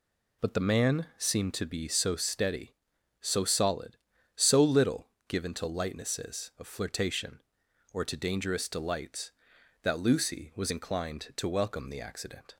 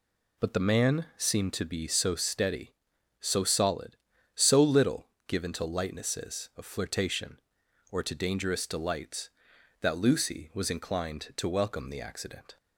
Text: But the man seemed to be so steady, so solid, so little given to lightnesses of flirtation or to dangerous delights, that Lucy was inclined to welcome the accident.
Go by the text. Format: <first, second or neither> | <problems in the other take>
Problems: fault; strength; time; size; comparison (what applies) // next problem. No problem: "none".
neither | pauses between "little" and "given"; slight; the same in both